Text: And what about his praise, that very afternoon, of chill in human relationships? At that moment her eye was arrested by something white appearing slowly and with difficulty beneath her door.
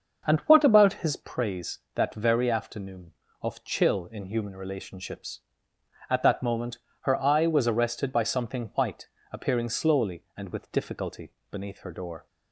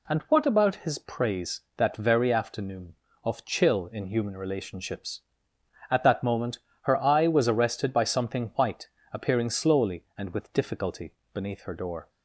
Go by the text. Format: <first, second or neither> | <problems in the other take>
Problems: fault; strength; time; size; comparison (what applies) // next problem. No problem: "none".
second | starts louder than the rest; until 1.3 s; 6.5 dB // pauses between "moment" and "her"; slight; at 6.7 s; 0.24 s long; slight in the second // pauses between "white" and "appearing"; slight; at 9.0 s; 0.24 s long; slight in the second // pauses between "difficulty" and "beneath"; slight; at 11.3 s; 0.18 s long; slight in the second